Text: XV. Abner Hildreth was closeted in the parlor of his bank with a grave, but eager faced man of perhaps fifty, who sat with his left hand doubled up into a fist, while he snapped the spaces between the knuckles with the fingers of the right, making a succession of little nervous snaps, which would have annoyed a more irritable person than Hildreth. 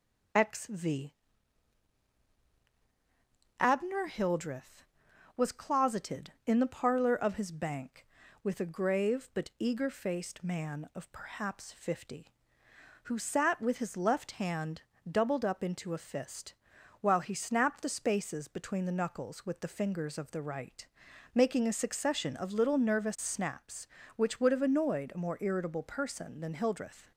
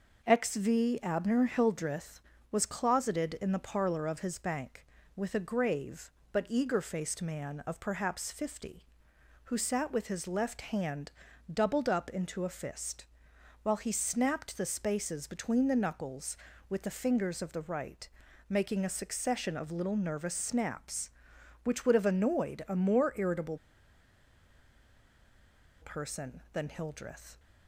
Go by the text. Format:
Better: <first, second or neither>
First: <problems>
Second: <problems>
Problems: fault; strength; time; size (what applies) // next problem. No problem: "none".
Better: first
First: pauses between "hand" and "doubled"; slight; at 14.8 s; 0.28 s long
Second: pauses between "hand" and "doubled"; at 11.0 s; 0.42 s long // pauses between "irritable" and "person"; strong; at 23.5 s; 2.2 s long